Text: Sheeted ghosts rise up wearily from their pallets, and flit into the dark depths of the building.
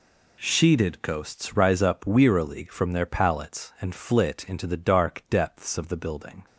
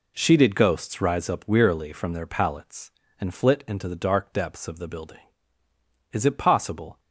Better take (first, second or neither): first